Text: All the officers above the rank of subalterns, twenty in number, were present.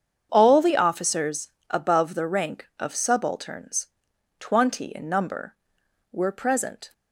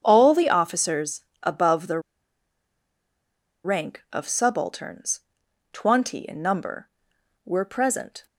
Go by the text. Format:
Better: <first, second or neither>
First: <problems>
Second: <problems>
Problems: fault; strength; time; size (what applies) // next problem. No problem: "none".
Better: first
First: starts louder than the rest; strong; until 1.3 s; 7.5 dB // pauses between "officers" and "above"; slight; at 1.4 s; 0.22 s long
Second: starts louder than the rest; strong; until 1.0 s; 7.5 dB // pauses between "officers" and "above"; slight; at 1.2 s; 0.22 s long // pauses between "the" and "rank"; strong; at 1.9 s; 1.6 s long